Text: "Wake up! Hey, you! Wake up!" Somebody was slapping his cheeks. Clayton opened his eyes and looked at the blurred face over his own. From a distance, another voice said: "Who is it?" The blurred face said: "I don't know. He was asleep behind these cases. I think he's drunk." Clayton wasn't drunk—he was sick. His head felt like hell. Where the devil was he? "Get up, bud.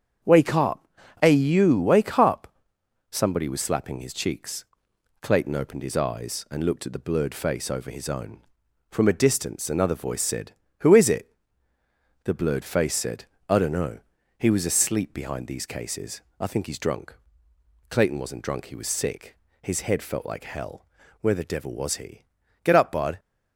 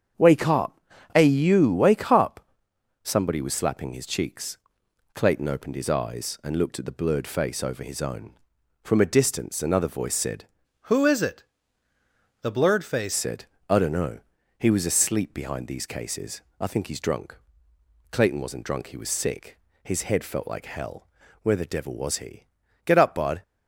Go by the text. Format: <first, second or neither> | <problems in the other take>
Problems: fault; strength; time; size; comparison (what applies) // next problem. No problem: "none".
first | starts louder than the rest; strong; until 1.5 s; 7.5 dB; strong in the first // changes voice from "Who" to "face"; from 10.8 to 13.1 s; 2.3 s long